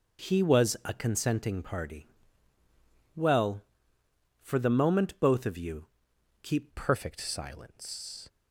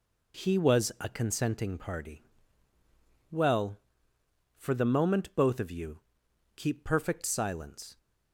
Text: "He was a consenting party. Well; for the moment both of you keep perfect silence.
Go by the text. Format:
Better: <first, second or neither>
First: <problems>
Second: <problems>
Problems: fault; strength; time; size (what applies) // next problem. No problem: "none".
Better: second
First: pauses between "you" and "keep"; noticeable; at 5.8 s; 0.56 s long // changes voice at "perfect"; from 6.7 s on; 1.5 s long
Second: pauses between "you" and "keep"; noticeable; at 5.9 s; 0.56 s long